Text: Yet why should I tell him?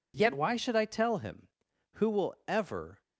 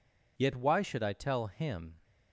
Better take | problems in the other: second | goes on to say "Who will ever"; noticeable; from 1.9 s on; 1.0 s long

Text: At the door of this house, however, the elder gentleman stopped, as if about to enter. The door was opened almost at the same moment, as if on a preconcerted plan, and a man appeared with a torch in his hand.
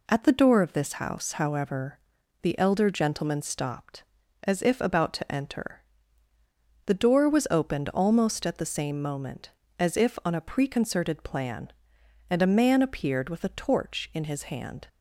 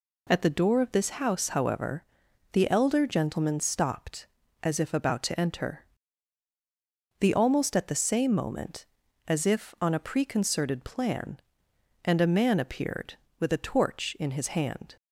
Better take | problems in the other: first | skips "door was opened"; at 7.3 s

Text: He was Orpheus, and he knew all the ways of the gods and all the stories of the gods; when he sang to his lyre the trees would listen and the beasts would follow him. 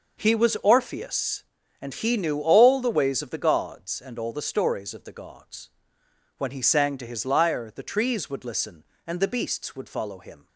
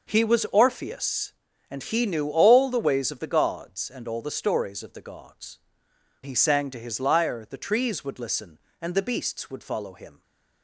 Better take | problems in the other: first | skips "when"; at 5.9 s

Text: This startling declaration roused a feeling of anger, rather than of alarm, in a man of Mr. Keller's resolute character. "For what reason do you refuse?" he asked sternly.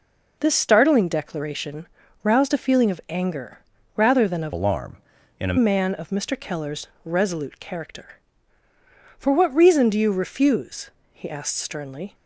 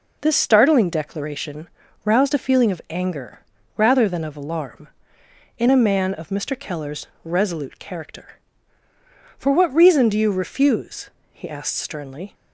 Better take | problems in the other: second | pauses between "declaration" and "roused"; slight; at 1.8 s; 0.36 s long; slight in the second // changes voice from "alarm" to "a"; from 4.5 to 5.5 s; 1.0 s long // pauses between "Keller's" and "resolute"; slight; at 6.8 s; 0.16 s long; slight in the second

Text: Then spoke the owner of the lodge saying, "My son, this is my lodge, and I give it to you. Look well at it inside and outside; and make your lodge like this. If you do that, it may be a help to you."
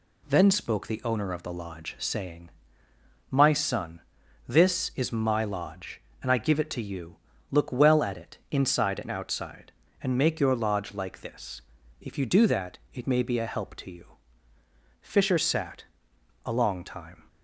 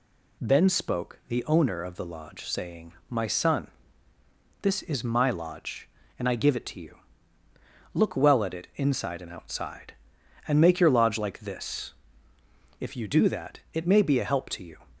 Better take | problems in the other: second | goes on to say "Fisher sat a long time"; strong; from 15.0 s on; 2.2 s long

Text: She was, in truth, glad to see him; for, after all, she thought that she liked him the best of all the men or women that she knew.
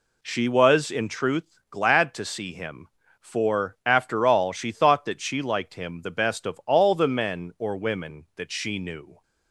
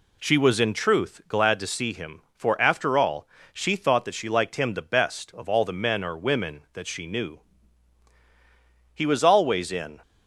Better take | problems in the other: first | goes on to say "He was always in"; noticeable; from 8.9 s on; 1.0 s long

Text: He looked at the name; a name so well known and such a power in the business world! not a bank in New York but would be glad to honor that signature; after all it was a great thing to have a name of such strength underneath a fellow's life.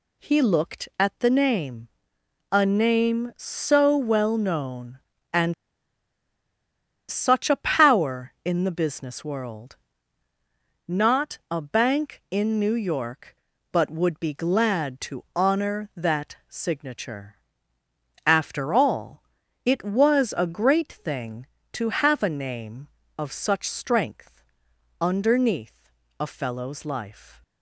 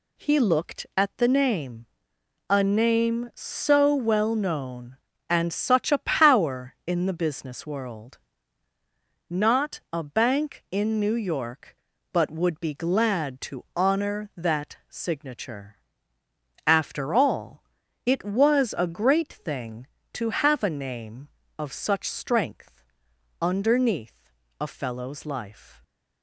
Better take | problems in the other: second | pauses between "and" and "such"; strong; at 5.5 s; 1.5 s long // pauses between "all" and "it"; at 19.2 s; 0.40 s long; also in the second // pauses between "strength" and "underneath"; noticeable; at 24.4 s; 0.56 s long; noticeable in the second // pauses between "underneath" and "a"; slight; at 25.9 s; 0.30 s long; slight in the second

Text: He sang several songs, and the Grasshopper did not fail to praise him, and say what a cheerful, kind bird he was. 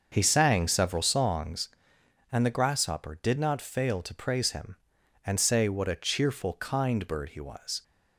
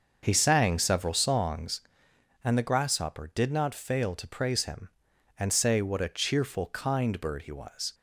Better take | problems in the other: neither | starts louder than the rest; the same in both

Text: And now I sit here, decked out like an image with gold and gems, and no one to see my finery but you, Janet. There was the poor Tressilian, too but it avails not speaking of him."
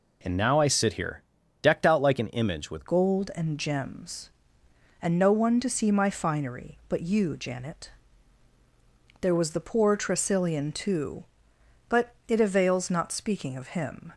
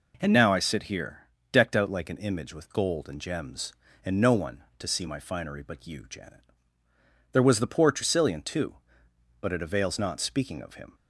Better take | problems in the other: second | changes voice at "gold"; from 2.8 s on; 11.3 s long // pauses between "but" and "it"; slight; at 12.0 s; 0.18 s long

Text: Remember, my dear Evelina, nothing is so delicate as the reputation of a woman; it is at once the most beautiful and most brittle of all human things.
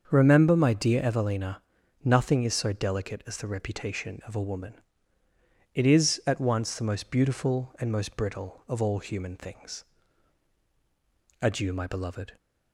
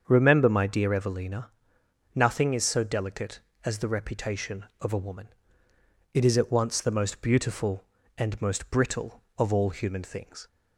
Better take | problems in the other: second | starts louder than the rest; until 1.1 s; 7 dB; strong in the second // goes on to say "Adieu my beloved"; noticeable; from 11.4 s on; 0.94 s long

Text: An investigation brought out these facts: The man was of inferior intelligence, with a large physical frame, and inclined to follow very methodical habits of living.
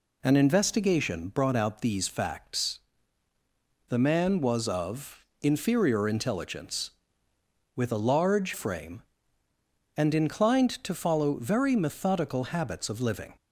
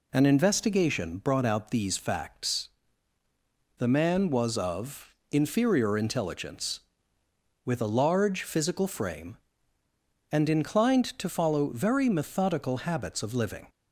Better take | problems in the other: second | pauses between "of" and "inferior"; slight; at 5.2 s; 0.16 s long; slight in the second // skips "physical"; at 8.5 s

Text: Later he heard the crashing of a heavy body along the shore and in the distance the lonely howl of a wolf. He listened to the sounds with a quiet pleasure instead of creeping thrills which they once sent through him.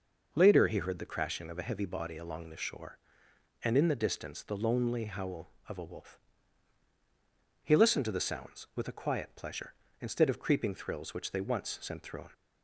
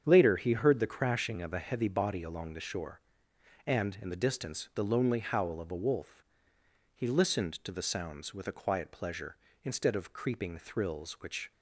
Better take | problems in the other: first | starts louder than the rest; strong; until 1.0 s; 7.5 dB // stops before "they once sent through him"; at 11.5 s

